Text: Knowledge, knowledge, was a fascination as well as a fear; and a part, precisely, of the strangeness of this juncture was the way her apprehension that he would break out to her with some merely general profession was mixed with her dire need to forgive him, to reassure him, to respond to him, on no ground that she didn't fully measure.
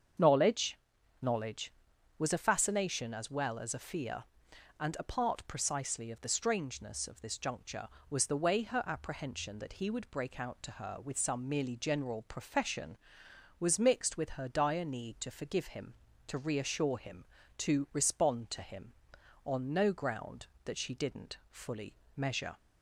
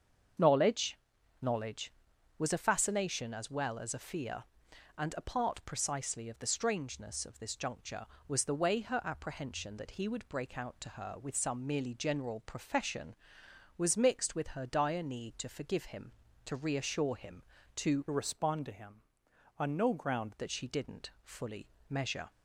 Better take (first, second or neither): first